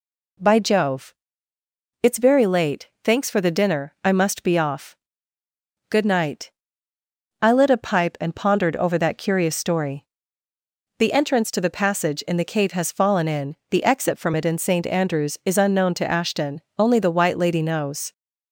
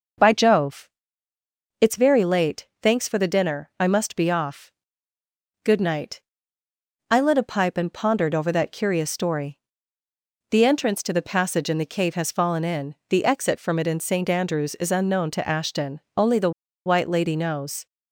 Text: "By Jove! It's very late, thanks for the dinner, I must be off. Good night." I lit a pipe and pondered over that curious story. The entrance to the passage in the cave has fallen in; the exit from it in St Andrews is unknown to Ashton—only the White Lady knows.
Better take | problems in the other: first | pauses between "the" and "White"; slight; at 16.5 s; 0.35 s long

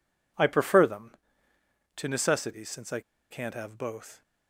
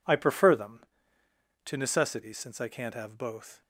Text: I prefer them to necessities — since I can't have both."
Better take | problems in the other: second | pauses between "I" and "can't"; slight; at 2.9 s; 0.32 s long

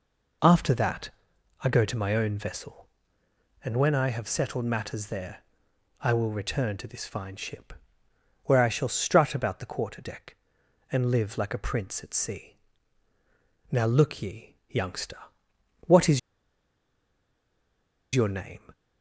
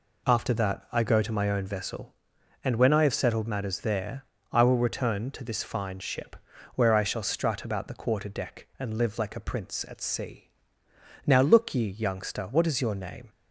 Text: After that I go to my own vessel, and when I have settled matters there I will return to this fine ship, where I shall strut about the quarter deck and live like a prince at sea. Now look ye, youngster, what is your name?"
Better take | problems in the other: second | pauses between "that" and "I"; noticeable; at 1.1 s; 0.52 s long // pauses between "there" and "I"; noticeable; at 5.4 s; 0.58 s long; slight in the second // pauses between "is" and "your"; strong; at 16.1 s; 1.9 s long

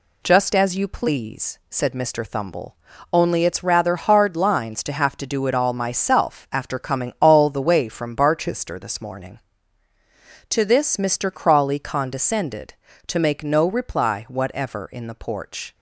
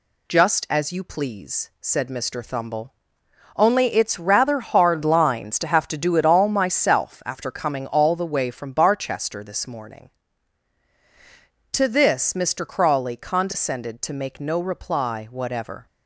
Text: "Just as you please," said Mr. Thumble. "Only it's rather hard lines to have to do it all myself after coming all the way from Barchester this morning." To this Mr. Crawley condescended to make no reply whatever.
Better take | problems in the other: second | goes on to say "In the porch"; noticeable; from 14.9 s on; 0.82 s long

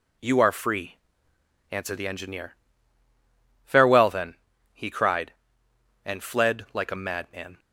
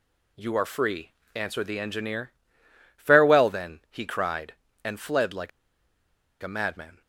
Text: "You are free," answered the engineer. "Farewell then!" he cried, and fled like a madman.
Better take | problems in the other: first | pauses between "like" and "a"; noticeable; at 5.5 s; 0.92 s long

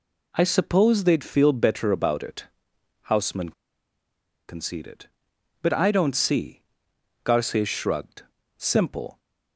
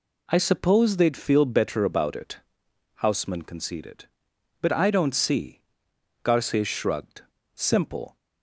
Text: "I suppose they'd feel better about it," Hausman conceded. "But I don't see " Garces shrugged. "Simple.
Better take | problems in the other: second | pauses between "Hausman" and "conceded"; noticeable; at 3.5 s; 0.95 s long

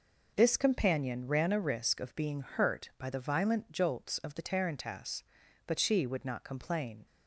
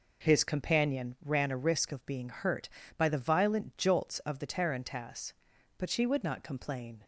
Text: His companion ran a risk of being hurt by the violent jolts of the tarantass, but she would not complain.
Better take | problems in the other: second | says "This" for "His"; at 0.3 s

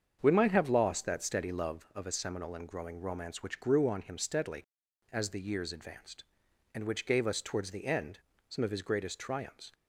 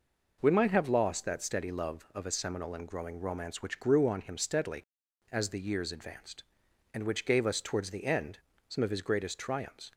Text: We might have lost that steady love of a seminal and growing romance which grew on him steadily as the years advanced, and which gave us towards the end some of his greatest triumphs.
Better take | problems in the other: second | starts louder than the rest; strong; until 1.8 s; 7 dB // pauses between "end" and "some"; slight; at 8.1 s; 0.30 s long; slight in the second

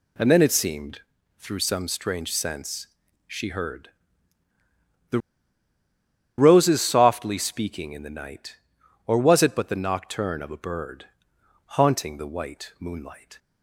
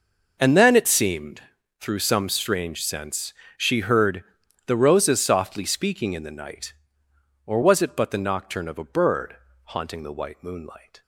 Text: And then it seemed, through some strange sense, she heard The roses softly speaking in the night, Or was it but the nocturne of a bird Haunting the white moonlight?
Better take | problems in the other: second | pauses between "heard" and "The"; at 3.8 s; 1.2 s long; also in the second // pauses between "The" and "roses"; at 5.1 s; 1.1 s long // pauses between "bird" and "Haunting"; noticeable; at 11.0 s; 0.60 s long; slight in the second

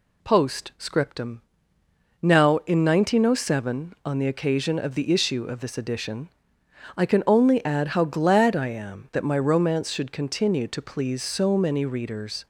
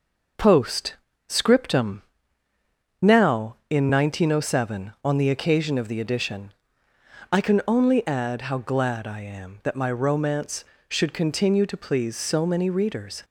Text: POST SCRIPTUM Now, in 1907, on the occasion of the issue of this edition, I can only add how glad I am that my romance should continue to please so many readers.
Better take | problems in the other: first | pauses between "POST" and "SCRIPTUM"; slight; at 0.9 s; 0.34 s long // pauses between "SCRIPTUM" and "Now"; at 2.0 s; 1.0 s long; noticeable in the first // skips "issue of this"; at 6.0 s

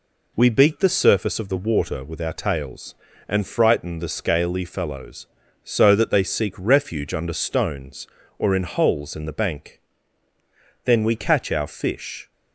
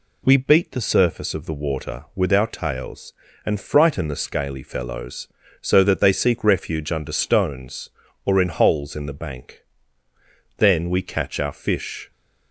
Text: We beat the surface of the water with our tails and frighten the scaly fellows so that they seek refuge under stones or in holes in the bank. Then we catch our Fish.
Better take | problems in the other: neither | none

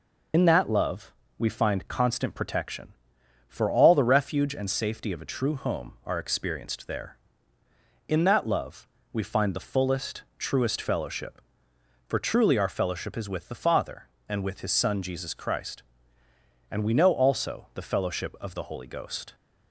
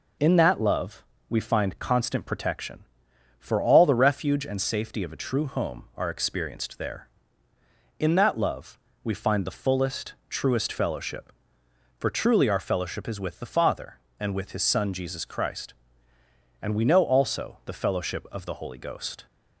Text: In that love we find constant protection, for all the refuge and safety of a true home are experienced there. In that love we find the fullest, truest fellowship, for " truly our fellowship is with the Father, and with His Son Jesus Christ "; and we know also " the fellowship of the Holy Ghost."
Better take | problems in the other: second | loses the start of "In"; at 0.3 s; 60 ms // pauses between "love" and "we"; slight; at 1.1 s; 0.26 s long; slight in the second // pauses between "love" and "we"; slight; at 8.8 s; 0.24 s long; slight in the second

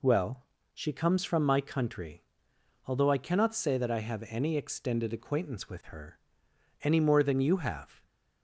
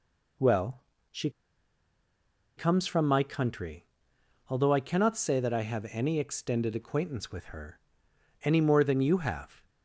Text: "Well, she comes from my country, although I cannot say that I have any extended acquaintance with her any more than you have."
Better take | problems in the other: first | pauses between "she" and "comes"; strong; at 1.2 s; 1.2 s long // pauses between "her" and "any"; noticeable; at 7.8 s; 0.64 s long; noticeable in the first

